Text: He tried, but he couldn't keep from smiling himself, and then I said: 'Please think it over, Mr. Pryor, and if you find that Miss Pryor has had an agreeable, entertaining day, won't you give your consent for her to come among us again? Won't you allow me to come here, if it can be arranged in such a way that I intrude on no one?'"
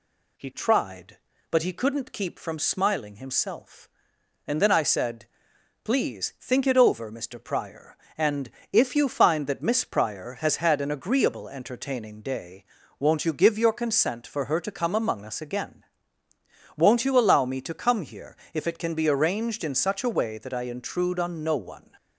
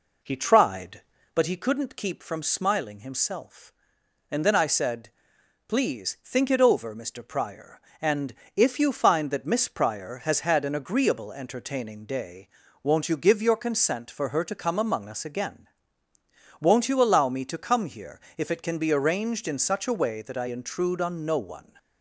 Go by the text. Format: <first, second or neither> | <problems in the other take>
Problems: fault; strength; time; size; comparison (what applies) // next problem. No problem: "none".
first | starts louder than the rest; until 1.4 s; 4 dB // pauses between "and" and "if"; slight; at 8.3 s; 0.22 s long; slight in the first